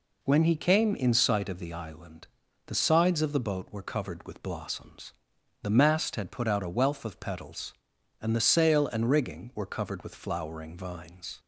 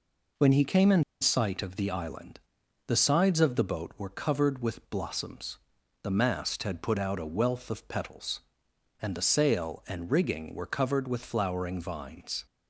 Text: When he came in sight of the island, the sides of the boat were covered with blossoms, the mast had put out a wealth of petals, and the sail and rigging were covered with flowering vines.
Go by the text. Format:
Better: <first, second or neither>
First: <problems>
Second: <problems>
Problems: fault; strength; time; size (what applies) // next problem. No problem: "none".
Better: first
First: none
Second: pauses between "in" and "sight"; slight; at 1.0 s; 0.19 s long